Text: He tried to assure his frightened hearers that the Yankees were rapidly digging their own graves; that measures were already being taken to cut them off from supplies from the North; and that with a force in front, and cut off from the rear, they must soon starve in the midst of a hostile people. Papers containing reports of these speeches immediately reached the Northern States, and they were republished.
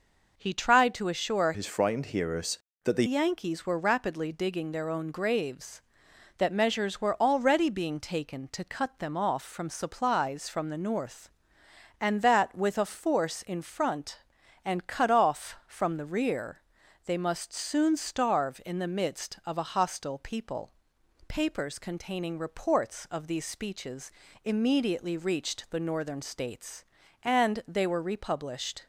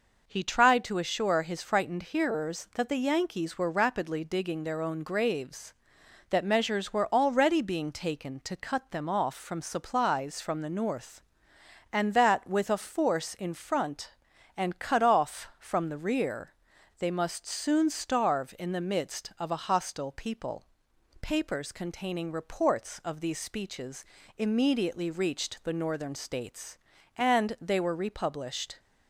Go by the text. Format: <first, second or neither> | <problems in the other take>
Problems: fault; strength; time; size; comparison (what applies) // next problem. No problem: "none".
second | changes voice from "his" to "the"; from 1.5 to 3.0 s; 1.5 s long // pauses between "speeches" and "immediately"; slight; at 24.0 s; 0.34 s long; slight in the second